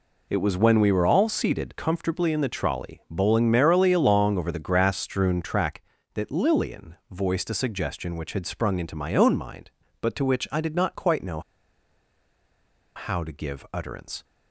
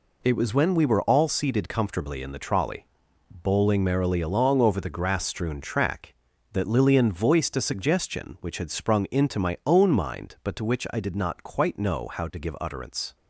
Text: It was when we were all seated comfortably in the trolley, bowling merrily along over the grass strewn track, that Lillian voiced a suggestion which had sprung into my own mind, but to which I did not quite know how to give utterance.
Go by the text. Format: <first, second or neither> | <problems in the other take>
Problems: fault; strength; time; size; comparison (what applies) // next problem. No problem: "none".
second | pauses between "know" and "how"; strong; at 11.3 s; 1.5 s long